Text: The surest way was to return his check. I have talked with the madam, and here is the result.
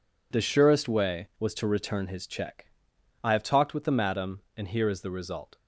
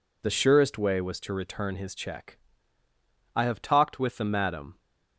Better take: first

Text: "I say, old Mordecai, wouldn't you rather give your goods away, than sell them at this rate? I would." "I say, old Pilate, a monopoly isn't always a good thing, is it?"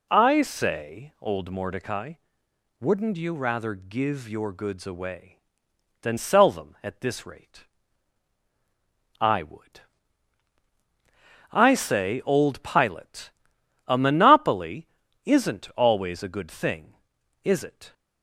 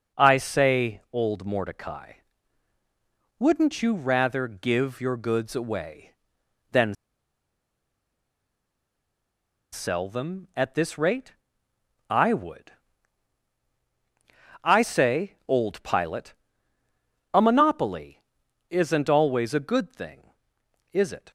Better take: first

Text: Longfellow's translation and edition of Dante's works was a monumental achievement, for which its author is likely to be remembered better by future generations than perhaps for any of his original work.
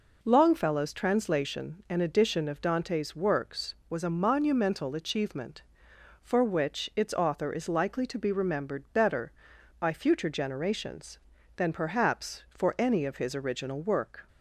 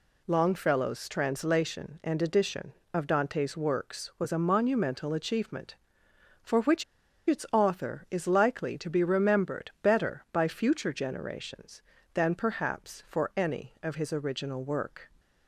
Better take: first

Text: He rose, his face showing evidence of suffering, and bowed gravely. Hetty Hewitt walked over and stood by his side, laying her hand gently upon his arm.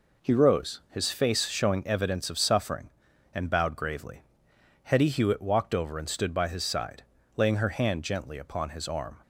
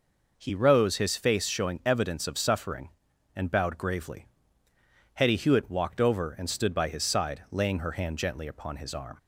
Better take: neither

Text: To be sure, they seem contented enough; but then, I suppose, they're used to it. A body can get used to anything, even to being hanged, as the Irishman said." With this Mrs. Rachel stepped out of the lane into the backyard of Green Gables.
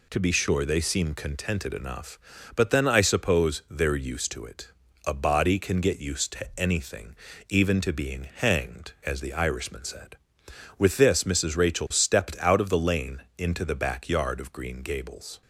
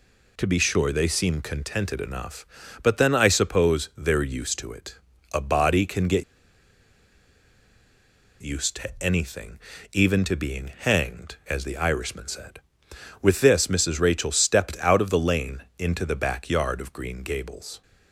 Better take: first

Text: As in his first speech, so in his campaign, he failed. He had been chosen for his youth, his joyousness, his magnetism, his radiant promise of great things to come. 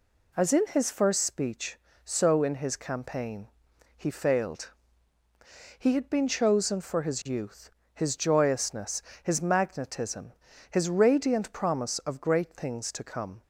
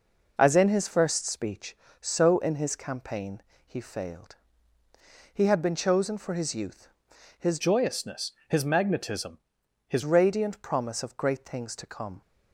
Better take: first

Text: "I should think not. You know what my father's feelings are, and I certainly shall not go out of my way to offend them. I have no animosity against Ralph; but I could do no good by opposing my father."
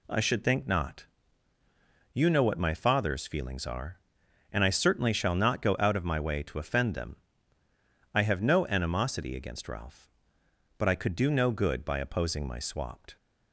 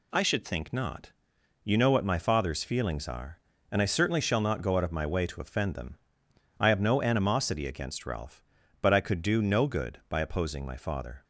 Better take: second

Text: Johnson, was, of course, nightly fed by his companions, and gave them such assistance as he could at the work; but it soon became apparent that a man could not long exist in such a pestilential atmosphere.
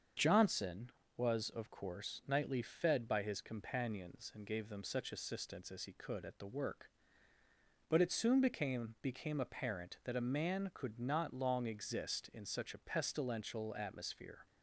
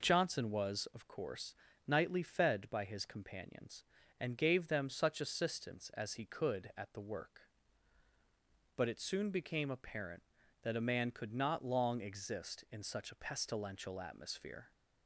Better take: second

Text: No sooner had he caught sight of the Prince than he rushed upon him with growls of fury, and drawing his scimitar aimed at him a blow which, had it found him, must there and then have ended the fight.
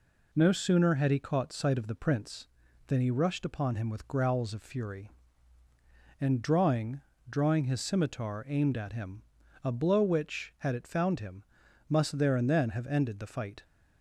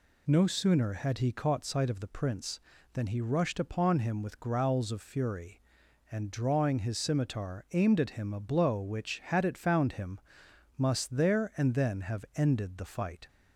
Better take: second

